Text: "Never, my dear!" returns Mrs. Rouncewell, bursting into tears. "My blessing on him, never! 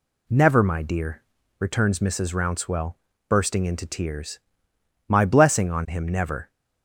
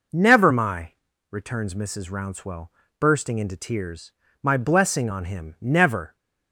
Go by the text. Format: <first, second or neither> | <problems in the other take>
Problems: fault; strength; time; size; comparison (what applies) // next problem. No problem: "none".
first | skips "dear"; at 1.1 s